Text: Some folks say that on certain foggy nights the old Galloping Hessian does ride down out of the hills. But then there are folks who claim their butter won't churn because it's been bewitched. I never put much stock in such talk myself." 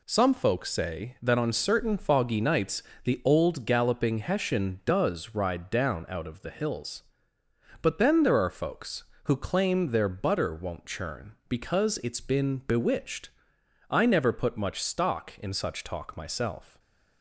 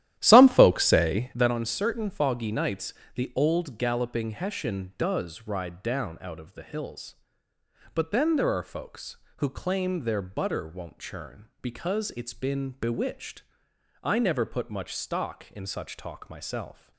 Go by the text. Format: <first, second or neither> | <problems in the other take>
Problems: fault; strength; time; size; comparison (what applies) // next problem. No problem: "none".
first | starts louder than the rest; strong; until 1.5 s; 12.5 dB // pauses between "nights" and "the"; slight; at 2.9 s; 0.22 s long; slight in the first